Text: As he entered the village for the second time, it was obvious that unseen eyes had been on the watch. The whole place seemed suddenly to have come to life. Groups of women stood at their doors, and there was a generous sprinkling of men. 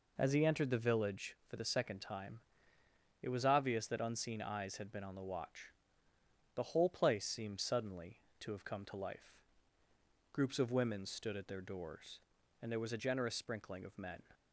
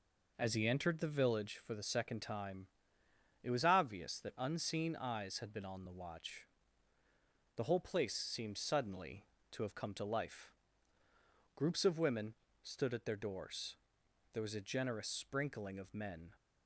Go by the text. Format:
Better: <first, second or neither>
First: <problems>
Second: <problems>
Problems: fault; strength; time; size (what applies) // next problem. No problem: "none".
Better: first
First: none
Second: pauses between "women" and "stood"; slight; at 12.3 s; 0.30 s long // skips "and"; at 14.0 s